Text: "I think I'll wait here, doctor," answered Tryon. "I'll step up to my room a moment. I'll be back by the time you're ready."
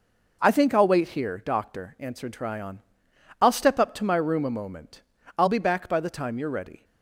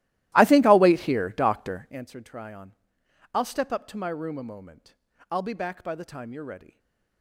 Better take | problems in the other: first | starts louder than the rest; strong; until 2.1 s; 16 dB // stays silent after the last word; slight; from 6.7 s on; 0.5 s long

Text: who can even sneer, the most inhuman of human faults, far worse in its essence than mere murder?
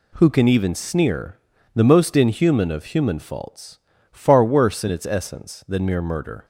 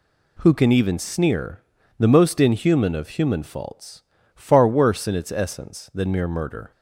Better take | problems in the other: neither | none

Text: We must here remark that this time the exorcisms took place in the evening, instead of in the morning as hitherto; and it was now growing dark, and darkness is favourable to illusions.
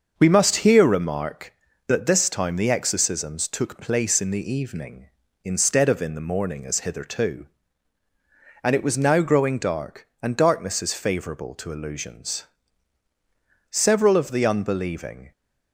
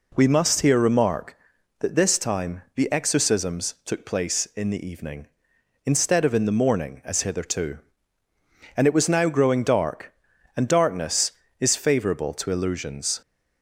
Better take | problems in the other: second | starts louder than the rest; until 1.2 s; 6.5 dB // goes on to say "Several of the unbelieving"; from 13.6 s on; 1.6 s long

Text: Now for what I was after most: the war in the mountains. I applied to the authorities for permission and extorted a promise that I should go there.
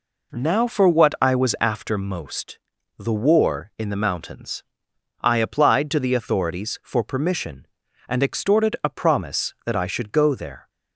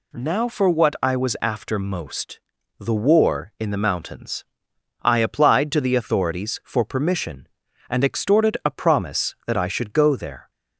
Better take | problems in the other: second | starts louder than the rest; noticeable; until 2.1 s; 4 dB

